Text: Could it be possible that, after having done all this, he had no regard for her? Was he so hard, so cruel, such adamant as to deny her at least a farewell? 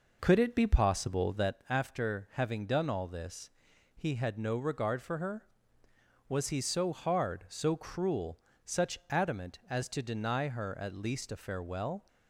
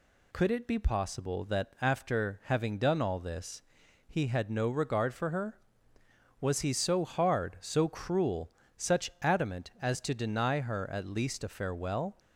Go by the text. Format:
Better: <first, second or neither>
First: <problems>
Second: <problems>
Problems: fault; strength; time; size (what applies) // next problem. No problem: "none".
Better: second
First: starts louder than the rest; noticeable; until 1.6 s; 4.5 dB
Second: none